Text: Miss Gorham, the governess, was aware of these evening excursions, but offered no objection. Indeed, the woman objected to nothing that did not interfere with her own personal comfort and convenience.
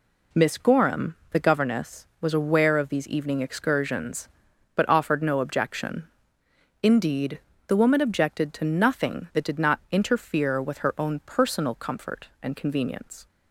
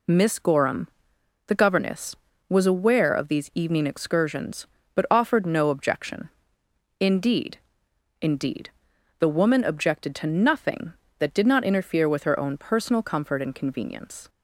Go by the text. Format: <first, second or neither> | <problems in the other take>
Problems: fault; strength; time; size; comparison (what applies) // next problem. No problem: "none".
first | says "Indeed" twice; at 8.2 s